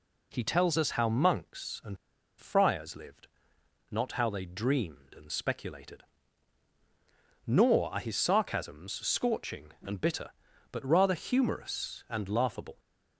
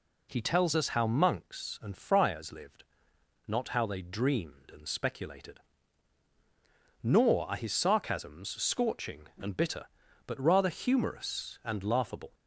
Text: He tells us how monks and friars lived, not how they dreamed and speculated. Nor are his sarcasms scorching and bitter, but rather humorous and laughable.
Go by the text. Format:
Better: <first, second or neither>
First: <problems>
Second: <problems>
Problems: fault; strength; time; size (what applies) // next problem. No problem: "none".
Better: second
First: pauses between "and" and "friars"; at 1.9 s; 0.44 s long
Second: none